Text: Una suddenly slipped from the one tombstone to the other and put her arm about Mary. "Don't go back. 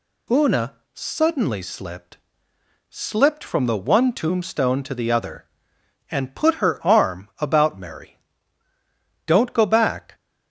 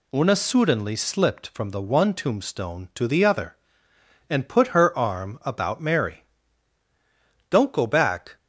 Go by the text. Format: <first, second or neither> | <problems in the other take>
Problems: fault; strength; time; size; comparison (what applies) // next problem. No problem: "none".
second | pauses between "Una" and "suddenly"; slight; at 0.7 s; 0.22 s long // says "slipped" twice; at 2.8 s